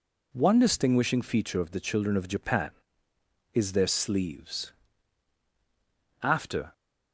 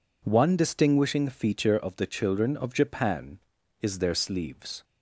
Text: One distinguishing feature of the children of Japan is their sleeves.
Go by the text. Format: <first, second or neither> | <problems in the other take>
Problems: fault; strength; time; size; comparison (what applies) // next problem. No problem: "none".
second | goes on to say "After"; from 6.2 s on; 0.50 s long